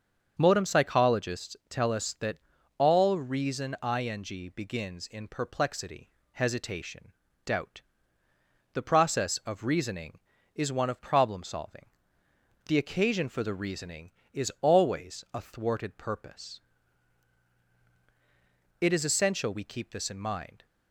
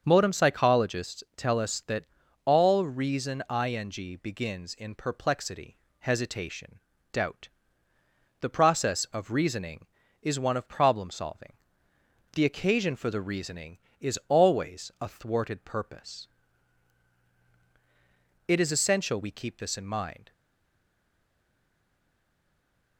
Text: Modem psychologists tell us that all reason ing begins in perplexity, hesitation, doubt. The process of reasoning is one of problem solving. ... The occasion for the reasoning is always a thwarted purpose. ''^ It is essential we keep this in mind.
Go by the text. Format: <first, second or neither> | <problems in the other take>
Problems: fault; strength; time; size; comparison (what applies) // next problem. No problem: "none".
first | starts louder than the rest; until 1.0 s; 6.5 dB; also in the first // pauses between "that" and "all"; at 2.0 s; 0.40 s long; also in the first // stays silent after the last word; strong; from 20.3 s on; 2.6 s long